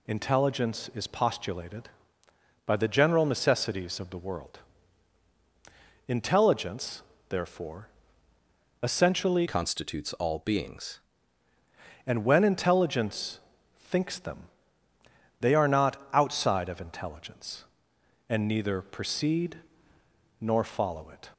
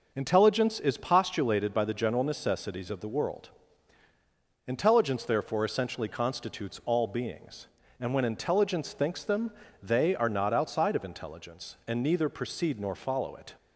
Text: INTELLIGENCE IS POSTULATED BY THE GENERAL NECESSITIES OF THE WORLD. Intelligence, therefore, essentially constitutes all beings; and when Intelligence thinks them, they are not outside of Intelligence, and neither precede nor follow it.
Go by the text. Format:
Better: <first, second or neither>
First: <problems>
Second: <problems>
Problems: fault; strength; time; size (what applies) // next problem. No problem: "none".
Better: second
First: changes voice from "constitutes" to "beings"; from 9.4 to 10.9 s; 1.5 s long // pauses between "Intelligence" and "thinks"; at 13.3 s; 0.40 s long // pauses between "not" and "outside"; slight; at 15.9 s; 0.18 s long // pauses between "precede" and "nor"; noticeable; at 19.5 s; 0.82 s long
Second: none